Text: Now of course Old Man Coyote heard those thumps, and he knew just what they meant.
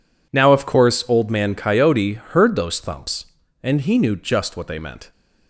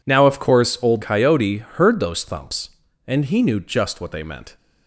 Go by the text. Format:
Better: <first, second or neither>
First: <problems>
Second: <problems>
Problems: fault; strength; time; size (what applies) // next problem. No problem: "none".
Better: first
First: none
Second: skips "Man"; at 1.0 s